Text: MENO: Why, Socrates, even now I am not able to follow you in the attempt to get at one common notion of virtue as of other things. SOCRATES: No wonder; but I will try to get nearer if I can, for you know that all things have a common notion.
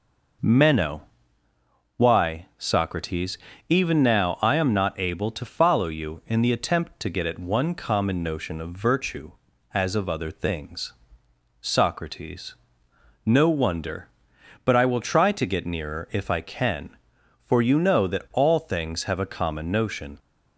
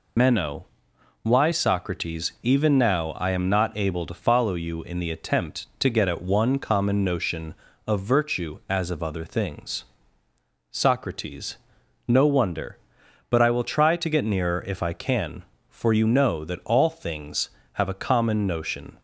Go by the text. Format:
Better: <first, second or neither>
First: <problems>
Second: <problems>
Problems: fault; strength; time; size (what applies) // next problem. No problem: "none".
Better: first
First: none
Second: loses the start of "MENO"; at 0.1 s; 90 ms